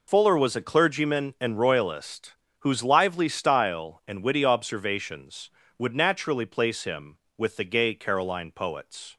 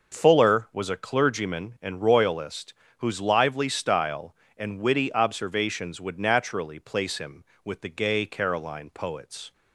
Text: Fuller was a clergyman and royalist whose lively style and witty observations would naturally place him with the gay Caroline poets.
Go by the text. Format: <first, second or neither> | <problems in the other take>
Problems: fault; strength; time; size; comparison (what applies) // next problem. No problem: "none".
second | loses the start of "Fuller"; at 0.0 s; 60 ms // pauses between "royalist" and "whose"; slight; at 2.3 s; 0.28 s long; slight in the second